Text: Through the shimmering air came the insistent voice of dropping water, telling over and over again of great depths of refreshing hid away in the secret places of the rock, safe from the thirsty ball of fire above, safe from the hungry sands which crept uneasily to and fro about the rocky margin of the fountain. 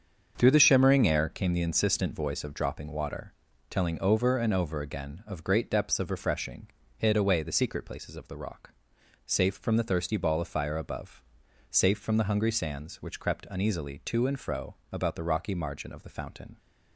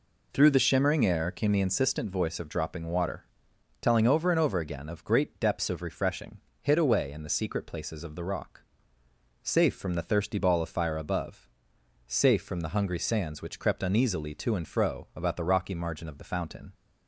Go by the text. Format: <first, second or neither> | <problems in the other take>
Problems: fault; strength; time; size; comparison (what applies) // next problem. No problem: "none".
second | starts louder than the rest; until 1.3 s; 7 dB // pauses between "refreshing" and "hid"; slight; at 6.6 s; 0.30 s long; slight in the second // skips "in"; at 7.4 s // pauses between "fro" and "about"; slight; at 14.7 s; 0.16 s long